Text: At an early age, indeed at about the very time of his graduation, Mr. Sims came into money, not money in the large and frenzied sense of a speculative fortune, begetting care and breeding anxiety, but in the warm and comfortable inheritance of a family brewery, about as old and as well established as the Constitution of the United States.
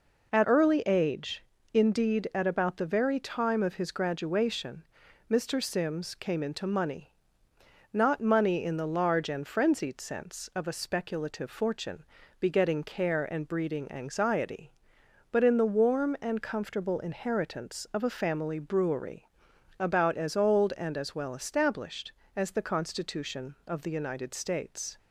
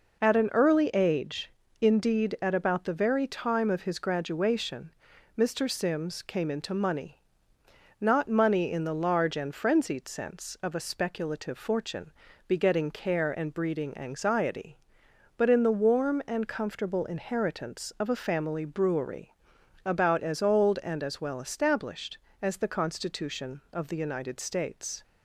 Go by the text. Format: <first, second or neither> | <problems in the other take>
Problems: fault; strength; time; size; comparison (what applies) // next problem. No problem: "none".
second | skips "an"; at 0.4 s